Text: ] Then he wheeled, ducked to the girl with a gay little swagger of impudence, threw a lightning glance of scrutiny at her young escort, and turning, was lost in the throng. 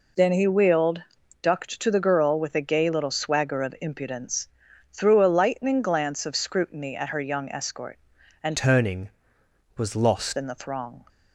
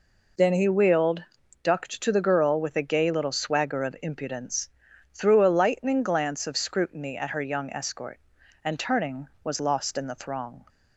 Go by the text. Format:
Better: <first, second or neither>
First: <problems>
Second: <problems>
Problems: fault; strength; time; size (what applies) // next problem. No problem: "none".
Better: second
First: changes voice from "turning" to "lost"; from 8.5 to 10.3 s; 1.8 s long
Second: none